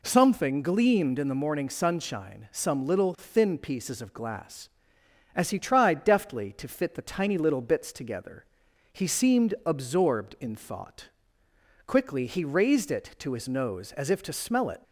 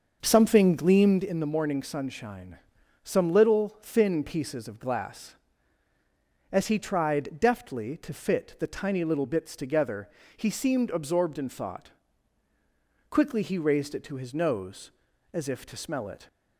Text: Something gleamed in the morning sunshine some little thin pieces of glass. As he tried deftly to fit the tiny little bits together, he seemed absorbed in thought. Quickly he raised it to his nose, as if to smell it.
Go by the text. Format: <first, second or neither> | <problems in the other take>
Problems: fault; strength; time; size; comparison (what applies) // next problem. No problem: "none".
first | starts louder than the rest; until 1.2 s; 6.5 dB // pauses between "sunshine" and "some"; at 2.5 s; 0.44 s long